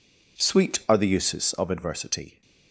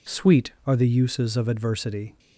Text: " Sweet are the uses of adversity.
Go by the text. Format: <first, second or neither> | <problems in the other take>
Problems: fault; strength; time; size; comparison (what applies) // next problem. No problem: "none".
first | changes voice at "Sweet"; from 0.0 s on; 2.1 s long